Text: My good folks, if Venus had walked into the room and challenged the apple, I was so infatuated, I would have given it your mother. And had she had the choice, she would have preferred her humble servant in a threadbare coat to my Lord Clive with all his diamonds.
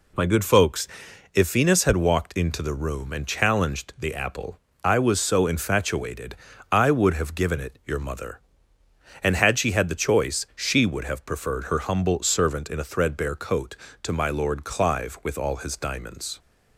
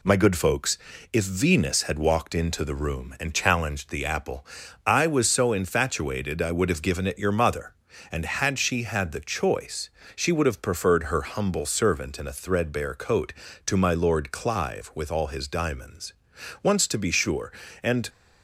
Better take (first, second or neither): first